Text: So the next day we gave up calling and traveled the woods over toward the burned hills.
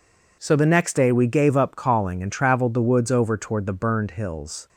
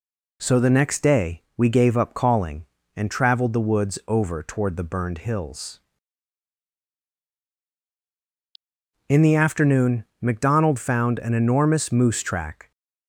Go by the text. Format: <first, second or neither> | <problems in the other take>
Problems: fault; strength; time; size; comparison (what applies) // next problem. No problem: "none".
first | goes on to say "In the afternoon McDonald found an enormous moose track"; strong; from 9.0 s on; 3.6 s long